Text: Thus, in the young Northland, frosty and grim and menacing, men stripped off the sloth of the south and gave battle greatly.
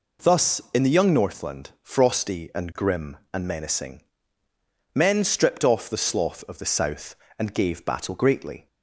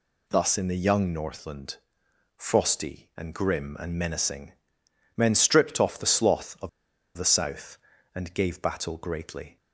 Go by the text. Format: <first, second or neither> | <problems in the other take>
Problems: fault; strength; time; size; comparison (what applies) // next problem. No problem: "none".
first | pauses between "of" and "the"; noticeable; at 6.6 s; 0.46 s long